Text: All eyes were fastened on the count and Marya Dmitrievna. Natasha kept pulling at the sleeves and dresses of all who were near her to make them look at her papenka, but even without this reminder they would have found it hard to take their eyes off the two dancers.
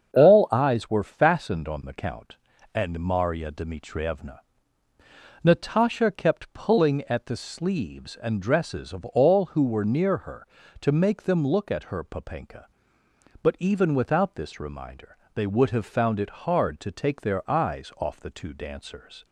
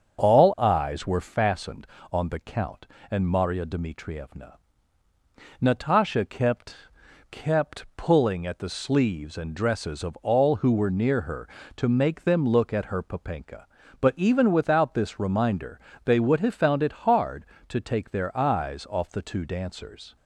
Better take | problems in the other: first | starts louder than the rest; until 1.2 s; 6.5 dB; strong in the first // says "kept" twice; at 7.2 s // pauses between "reminder" and "they"; slight; at 15.7 s; 0.28 s long; slight in the first

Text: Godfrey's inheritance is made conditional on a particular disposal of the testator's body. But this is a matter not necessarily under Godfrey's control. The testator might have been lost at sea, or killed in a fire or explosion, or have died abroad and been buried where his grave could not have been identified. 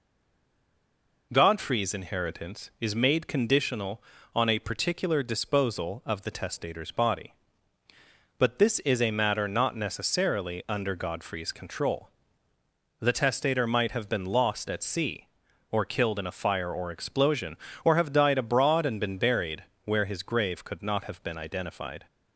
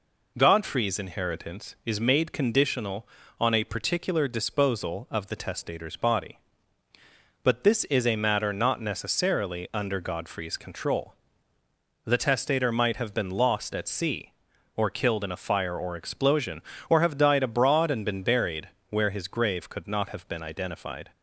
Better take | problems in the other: second | stays silent before the first word; noticeable; until 1.3 s; 1.3 s long // pauses between "buried" and "where"; slight; at 19.6 s; 0.20 s long; slight in the second

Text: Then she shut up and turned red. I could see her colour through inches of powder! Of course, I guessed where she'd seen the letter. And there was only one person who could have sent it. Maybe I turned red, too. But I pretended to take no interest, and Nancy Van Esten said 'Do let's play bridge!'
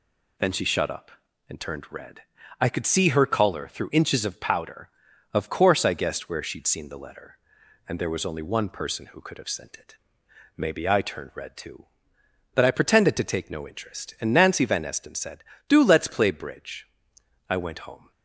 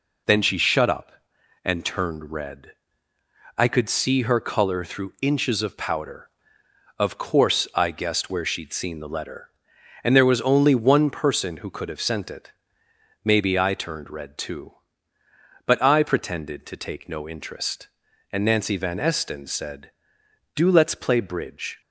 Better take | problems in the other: second | goes on to say "I went home"; noticeable; from 17.4 s on; 0.62 s long

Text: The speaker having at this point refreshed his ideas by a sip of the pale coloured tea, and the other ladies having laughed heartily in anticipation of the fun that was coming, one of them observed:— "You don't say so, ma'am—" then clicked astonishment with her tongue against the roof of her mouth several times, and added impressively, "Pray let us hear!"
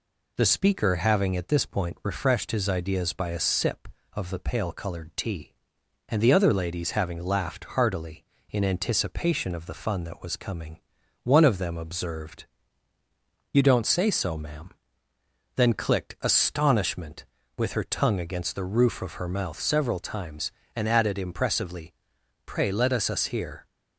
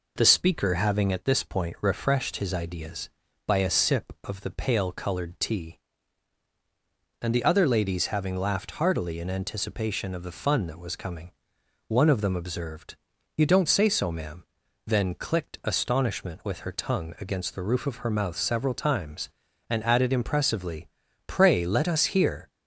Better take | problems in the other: second | says "us" twice; at 23.0 s

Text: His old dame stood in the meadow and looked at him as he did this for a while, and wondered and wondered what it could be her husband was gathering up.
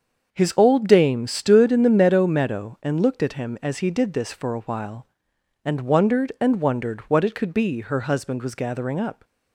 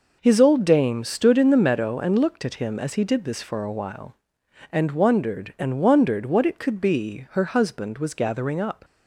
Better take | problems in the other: second | starts louder than the rest; until 1.3 s; 6.5 dB // says "meadow" twice; at 2.2 s

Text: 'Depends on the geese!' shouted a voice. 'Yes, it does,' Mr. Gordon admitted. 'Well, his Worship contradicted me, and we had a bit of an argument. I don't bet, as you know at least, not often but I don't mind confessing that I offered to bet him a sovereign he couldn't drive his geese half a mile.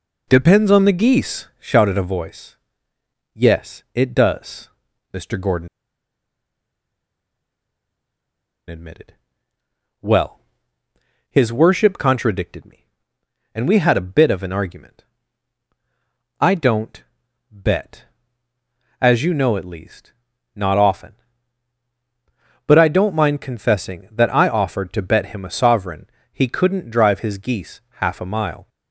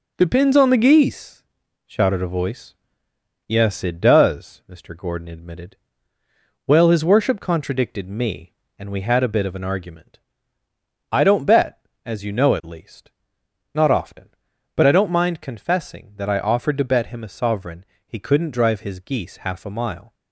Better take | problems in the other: second | pauses between "Gordon" and "admitted"; strong; at 5.6 s; 3.0 s long // pauses between "don't" and "bet"; noticeable; at 17.0 s; 0.48 s long // pauses between "sovereign" and "he"; slight; at 26.0 s; 0.24 s long; slight in the second

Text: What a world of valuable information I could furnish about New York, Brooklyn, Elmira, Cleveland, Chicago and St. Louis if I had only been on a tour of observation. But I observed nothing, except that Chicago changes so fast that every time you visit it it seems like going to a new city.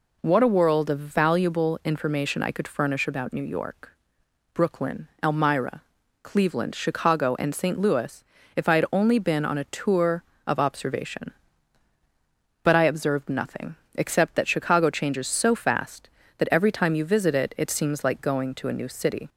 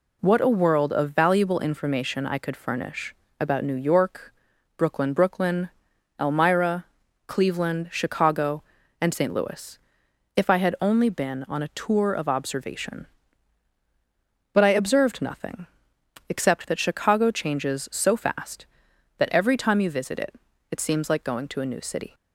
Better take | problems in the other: first | pauses between "furnish" and "about"; slight; at 3.1 s; 0.26 s long // says "Brooklyn" twice; at 5.1 s // pauses between "Louis" and "if"; noticeable; at 9.7 s; 0.58 s long; slight in the first // pauses between "it" and "it"; slight; at 20.3 s; 0.36 s long

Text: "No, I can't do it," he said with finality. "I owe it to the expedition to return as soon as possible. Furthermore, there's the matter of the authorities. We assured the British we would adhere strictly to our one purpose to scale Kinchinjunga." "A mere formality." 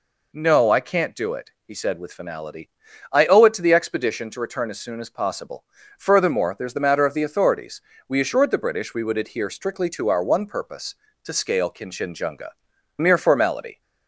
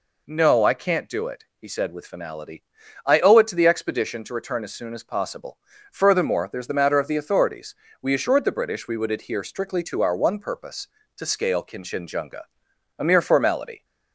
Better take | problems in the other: second | skips "A"; at 12.7 s

